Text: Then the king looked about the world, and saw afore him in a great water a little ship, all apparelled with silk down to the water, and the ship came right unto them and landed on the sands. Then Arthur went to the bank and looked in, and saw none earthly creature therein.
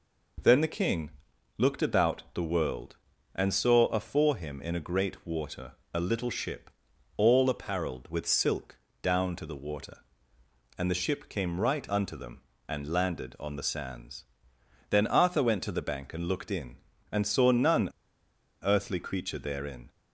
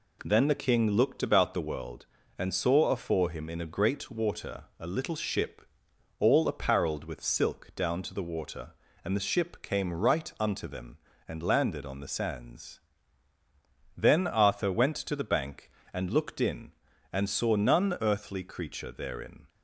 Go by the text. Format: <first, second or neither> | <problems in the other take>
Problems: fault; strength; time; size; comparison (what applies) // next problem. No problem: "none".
second | pauses between "king" and "looked"; noticeable; at 1.1 s; 0.46 s long // pauses between "water" and "a"; slight; at 5.7 s; 0.20 s long // pauses between "silk" and "down"; slight; at 8.7 s; 0.24 s long // pauses between "none" and "earthly"; noticeable; at 17.8 s; 0.73 s long